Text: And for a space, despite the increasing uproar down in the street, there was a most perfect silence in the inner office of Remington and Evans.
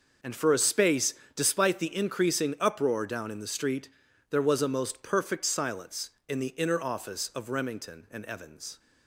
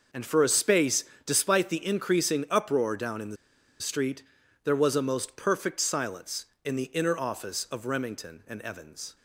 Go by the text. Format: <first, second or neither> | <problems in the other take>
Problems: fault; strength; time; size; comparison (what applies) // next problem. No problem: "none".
first | pauses between "the" and "street"; at 3.3 s; 0.44 s long